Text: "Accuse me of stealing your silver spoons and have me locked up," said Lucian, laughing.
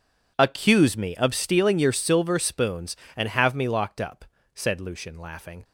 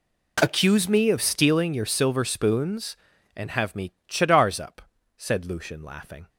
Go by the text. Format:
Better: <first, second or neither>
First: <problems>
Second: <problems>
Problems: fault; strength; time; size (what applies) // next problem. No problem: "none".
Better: first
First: none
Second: says "chadars" for "locked"; at 4.0 s